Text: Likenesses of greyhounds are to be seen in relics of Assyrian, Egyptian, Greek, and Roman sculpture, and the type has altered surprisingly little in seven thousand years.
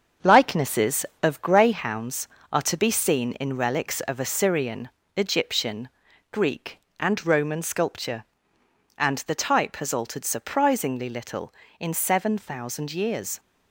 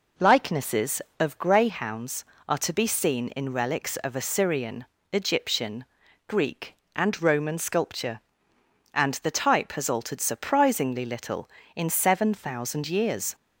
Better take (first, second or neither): second